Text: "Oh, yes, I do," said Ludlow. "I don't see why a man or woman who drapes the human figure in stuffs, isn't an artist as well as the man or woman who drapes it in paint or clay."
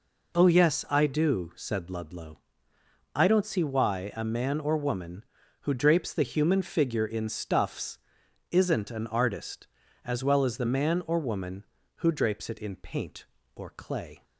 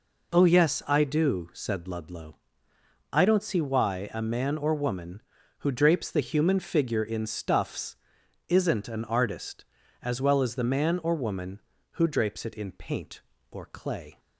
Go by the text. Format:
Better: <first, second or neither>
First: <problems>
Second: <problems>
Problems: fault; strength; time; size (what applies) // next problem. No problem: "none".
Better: neither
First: none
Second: none